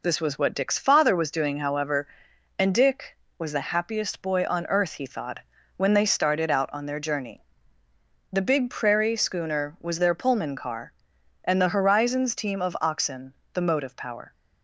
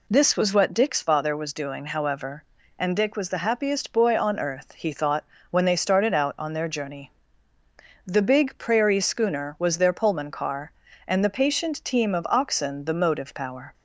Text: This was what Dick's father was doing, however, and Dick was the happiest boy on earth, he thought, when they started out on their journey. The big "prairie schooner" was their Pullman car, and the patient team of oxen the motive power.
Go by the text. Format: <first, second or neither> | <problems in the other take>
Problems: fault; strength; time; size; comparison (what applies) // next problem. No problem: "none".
second | says "horizons" for "patient"; at 11.6 s // pauses between "oxen" and "the"; slight; at 13.3 s; 0.18 s long